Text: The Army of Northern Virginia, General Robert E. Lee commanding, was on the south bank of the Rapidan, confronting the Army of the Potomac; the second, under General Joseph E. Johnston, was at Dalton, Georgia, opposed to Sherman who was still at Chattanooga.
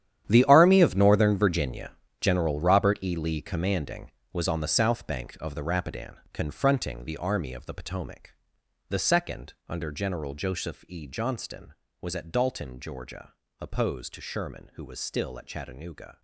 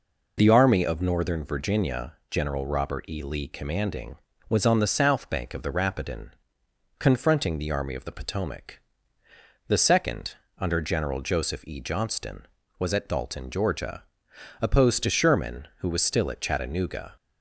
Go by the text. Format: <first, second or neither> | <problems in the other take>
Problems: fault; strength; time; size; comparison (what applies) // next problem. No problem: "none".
second | gets quieter; strong; throughout; 14 dB